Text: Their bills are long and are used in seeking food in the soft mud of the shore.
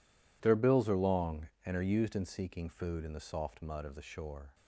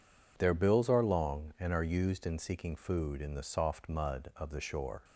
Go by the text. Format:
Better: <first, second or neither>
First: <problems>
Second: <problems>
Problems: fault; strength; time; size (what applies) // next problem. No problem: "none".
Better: neither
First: none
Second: none